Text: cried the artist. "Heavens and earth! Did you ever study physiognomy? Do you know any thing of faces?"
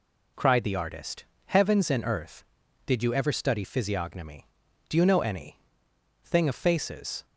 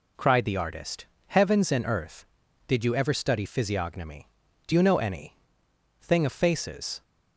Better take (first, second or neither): neither